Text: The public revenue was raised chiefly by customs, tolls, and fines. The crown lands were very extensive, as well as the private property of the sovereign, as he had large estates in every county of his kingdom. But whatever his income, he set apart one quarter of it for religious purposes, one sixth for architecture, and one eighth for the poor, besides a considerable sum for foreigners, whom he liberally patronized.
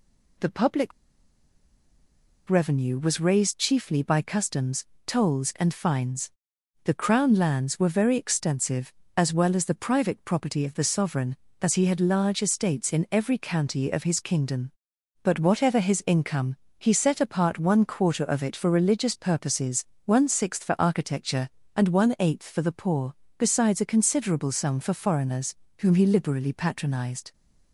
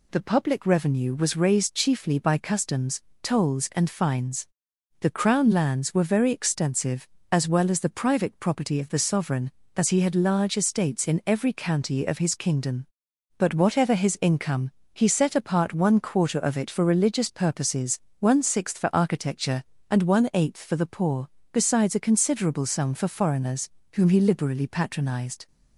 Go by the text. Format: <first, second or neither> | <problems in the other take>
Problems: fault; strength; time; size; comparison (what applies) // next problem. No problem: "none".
second | pauses between "public" and "revenue"; strong; at 0.9 s; 1.5 s long